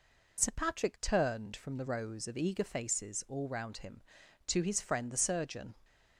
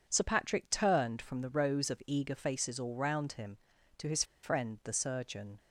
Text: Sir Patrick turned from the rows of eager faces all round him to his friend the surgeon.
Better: first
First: none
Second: pauses between "his" and "friend"; slight; at 4.2 s; 0.19 s long

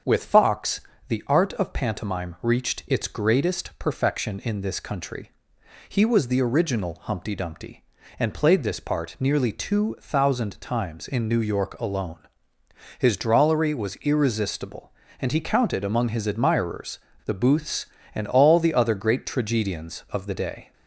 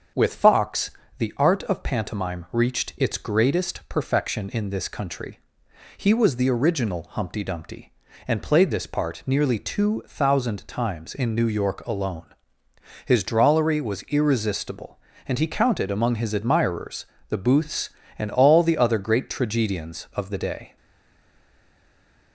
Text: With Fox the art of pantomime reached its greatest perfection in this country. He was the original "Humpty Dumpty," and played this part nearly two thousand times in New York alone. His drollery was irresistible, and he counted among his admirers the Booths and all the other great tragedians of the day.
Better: first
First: starts louder than the rest; until 1.3 s; 7 dB // pauses between "Fox" and "the"; slight; at 0.8 s; 0.28 s long // pauses between "admirers" and "the"; slight; at 16.9 s; 0.27 s long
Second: starts louder than the rest; until 1.4 s; 7 dB // pauses between "Fox" and "the"; slight; at 0.9 s; 0.28 s long // pauses between "admirers" and "the"; slight; at 17.0 s; 0.24 s long // stays silent after the last word; noticeable; from 20.7 s on; 1.6 s long

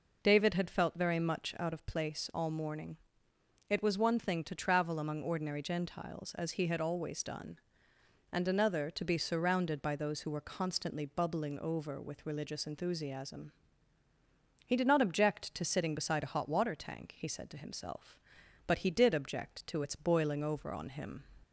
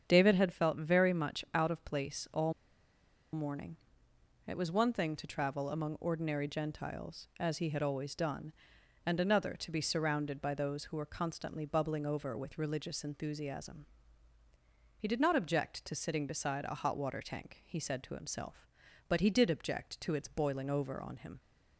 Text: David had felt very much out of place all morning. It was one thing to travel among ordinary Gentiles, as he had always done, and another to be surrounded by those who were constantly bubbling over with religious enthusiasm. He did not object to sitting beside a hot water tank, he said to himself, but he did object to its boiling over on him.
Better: first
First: none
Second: starts louder than the rest; strong; until 1.1 s; 7.5 dB // pauses between "all" and "morning"; noticeable; at 2.5 s; 0.81 s long

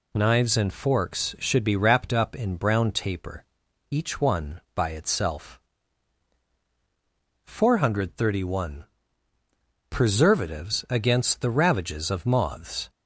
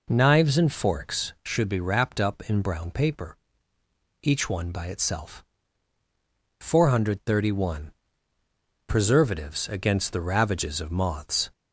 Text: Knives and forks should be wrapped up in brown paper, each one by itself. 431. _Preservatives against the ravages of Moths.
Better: second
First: says "taper" for "paper"; at 2.9 s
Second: none

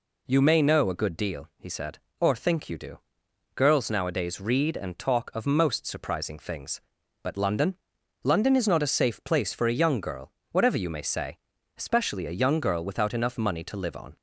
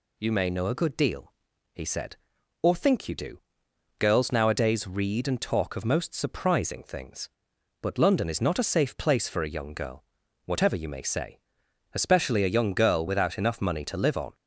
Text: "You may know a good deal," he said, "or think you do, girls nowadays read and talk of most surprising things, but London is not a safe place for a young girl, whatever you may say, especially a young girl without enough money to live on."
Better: second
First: says "London" twice; at 8.2 s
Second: none

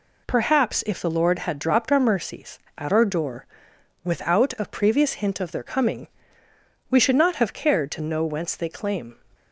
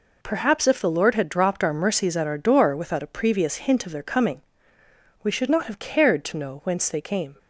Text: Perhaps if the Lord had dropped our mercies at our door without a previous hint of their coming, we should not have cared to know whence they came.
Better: second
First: pauses between "door" and "without"; noticeable; at 3.4 s; 0.60 s long // says "claim" for "came"; at 8.7 s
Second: none

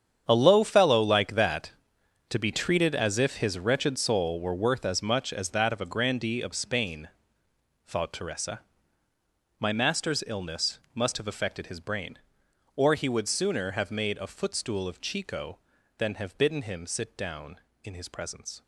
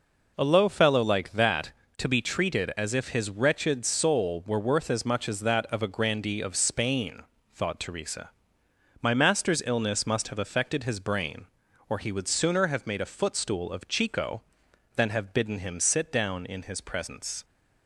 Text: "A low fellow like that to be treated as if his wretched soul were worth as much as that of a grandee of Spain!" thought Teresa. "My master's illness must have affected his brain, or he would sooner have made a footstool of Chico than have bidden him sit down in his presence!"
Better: second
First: gets quieter; strong; throughout; 14.5 dB // pauses between "illness" and "must"; slight; at 10.8 s; 0.16 s long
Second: none

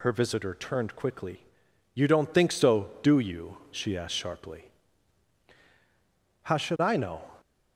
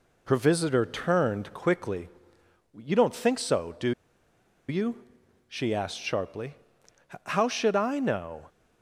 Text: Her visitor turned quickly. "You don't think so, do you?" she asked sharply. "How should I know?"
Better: first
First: none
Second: pauses between "do" and "you"; noticeable; at 3.9 s; 0.77 s long

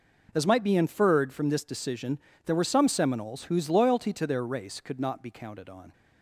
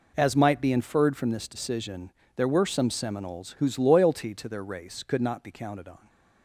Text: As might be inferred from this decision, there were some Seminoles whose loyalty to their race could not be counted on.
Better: neither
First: none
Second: none

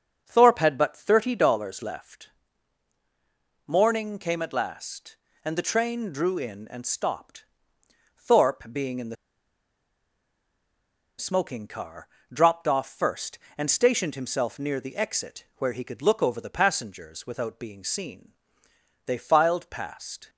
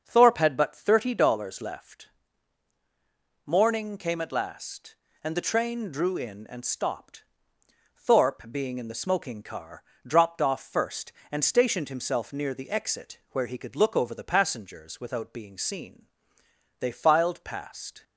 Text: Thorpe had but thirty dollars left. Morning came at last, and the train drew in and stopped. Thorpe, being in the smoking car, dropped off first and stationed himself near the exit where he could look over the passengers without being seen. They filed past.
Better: second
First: starts louder than the rest; until 1.2 s; 7 dB // pauses between "the" and "smoking"; strong; at 9.1 s; 2.0 s long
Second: starts louder than the rest; until 1.0 s; 7 dB

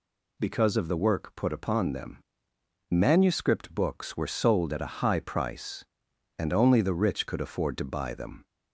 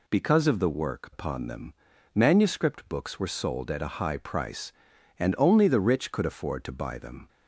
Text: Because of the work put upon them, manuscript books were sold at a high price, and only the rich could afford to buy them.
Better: first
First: none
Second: skips "put"; at 1.1 s

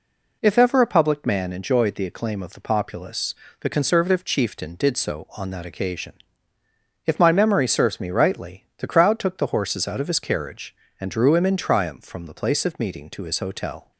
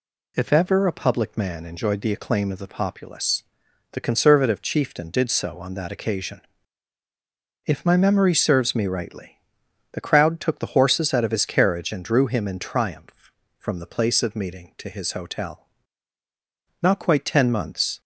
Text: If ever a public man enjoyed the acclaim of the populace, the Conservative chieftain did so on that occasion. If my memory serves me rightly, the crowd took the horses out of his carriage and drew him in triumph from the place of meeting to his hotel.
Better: first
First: none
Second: goes on to say "Not quite ten months"; noticeable; from 16.8 s on; 1.1 s long

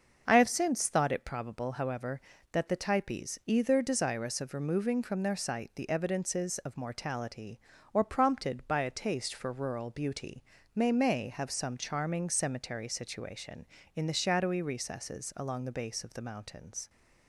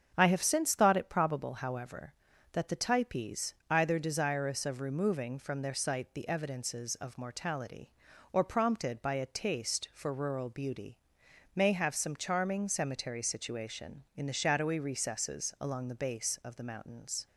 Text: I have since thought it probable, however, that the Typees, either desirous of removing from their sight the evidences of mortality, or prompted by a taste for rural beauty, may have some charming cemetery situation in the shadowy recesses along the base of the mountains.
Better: second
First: starts louder than the rest; until 1.2 s; 6.5 dB // says "may" twice; at 10.9 s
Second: starts louder than the rest; strong; until 1.1 s; 7 dB

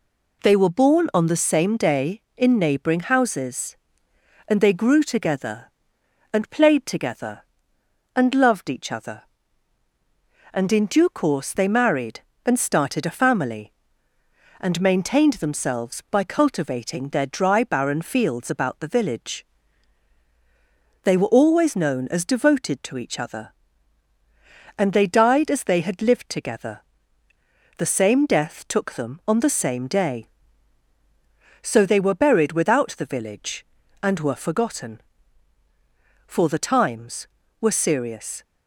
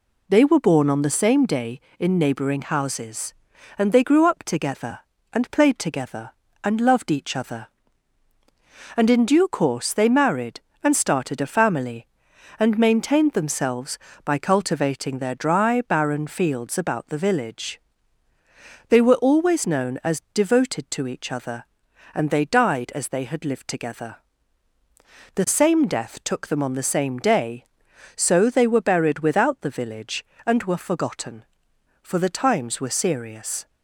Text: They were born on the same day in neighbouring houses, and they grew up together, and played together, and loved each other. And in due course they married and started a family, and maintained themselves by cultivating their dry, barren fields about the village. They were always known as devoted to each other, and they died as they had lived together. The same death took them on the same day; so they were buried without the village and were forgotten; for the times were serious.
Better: second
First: skips "up"; at 5.0 s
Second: none

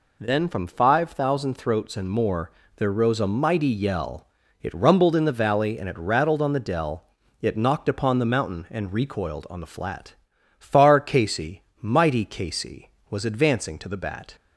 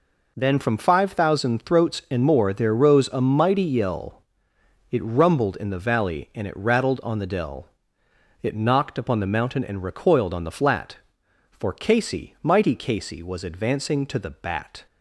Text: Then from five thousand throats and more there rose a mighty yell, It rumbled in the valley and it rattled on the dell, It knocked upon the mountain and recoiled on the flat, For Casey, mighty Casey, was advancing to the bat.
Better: second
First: pauses between "more" and "there"; slight; at 2.5 s; 0.26 s long // says "Far" for "For"; at 10.5 s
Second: none

